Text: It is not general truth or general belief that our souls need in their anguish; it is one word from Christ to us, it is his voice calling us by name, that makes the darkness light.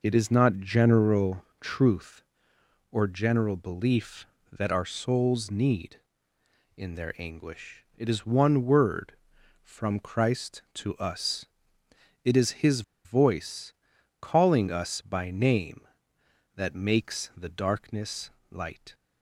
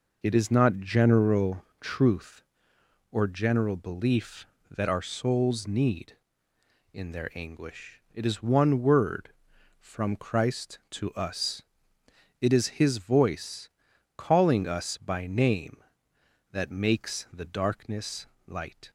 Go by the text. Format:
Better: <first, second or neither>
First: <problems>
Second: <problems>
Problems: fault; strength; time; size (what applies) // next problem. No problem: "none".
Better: second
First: pauses between "general" and "truth"; slight; at 1.4 s; 0.16 s long // pauses between "his" and "voice"; slight; at 12.8 s; 0.23 s long // pauses between "voice" and "calling"; noticeable; at 13.7 s; 0.46 s long // pauses between "darkness" and "light"; slight; at 18.2 s; 0.22 s long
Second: pauses between "general" and "truth"; slight; at 1.6 s; 0.16 s long // pauses between "voice" and "calling"; noticeable; at 13.6 s; 0.46 s long // pauses between "darkness" and "light"; slight; at 18.2 s; 0.22 s long